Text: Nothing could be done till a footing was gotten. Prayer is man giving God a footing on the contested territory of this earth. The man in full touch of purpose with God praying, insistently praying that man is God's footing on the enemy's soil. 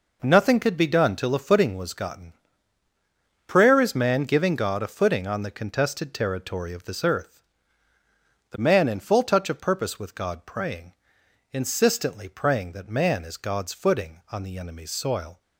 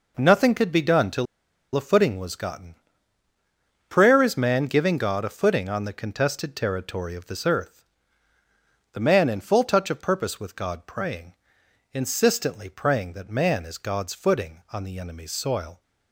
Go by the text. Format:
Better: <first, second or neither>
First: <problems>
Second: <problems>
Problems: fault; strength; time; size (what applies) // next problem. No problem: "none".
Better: first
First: none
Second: pauses between "till" and "a"; noticeable; at 1.2 s; 0.50 s long